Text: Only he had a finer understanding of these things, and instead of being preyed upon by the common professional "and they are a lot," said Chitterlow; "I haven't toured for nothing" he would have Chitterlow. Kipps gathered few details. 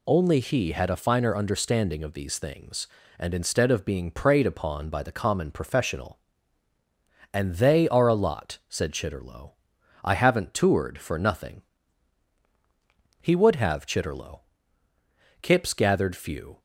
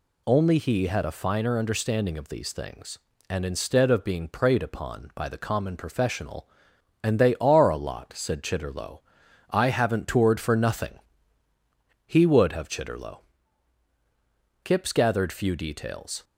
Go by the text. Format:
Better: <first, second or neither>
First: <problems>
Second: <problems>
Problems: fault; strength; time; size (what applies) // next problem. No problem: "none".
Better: second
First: pauses between "nothing" and "he"; strong; at 11.6 s; 1.5 s long // stops before "details"; at 16.5 s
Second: pauses between "nothing" and "he"; at 10.9 s; 1.0 s long